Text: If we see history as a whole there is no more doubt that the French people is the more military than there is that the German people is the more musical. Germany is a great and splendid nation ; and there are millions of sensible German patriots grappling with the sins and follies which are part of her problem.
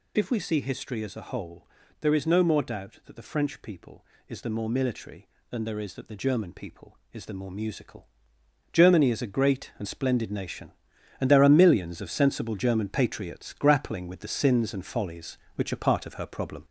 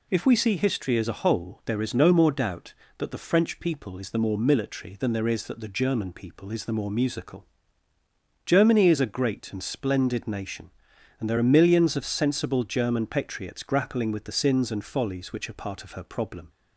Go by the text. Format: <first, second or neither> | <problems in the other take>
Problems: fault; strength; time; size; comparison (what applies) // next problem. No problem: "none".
second | gets louder; throughout; 3.5 dB // pauses between "whole" and "there"; slight; at 1.6 s; 0.32 s long